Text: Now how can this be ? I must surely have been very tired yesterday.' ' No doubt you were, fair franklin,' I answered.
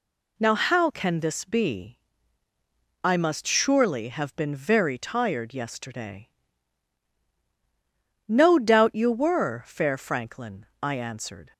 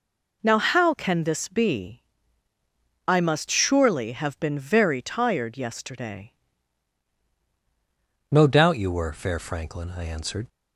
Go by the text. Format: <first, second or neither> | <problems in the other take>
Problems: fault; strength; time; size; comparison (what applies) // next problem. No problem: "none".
first | changes voice at "No"; from 8.3 s on; 2.1 s long